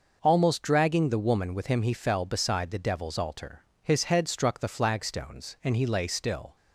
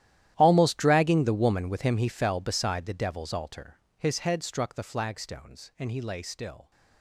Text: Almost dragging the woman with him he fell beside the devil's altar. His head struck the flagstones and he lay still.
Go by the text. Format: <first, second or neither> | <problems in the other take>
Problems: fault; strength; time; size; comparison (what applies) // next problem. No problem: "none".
first | gets quieter; strong; throughout; 19 dB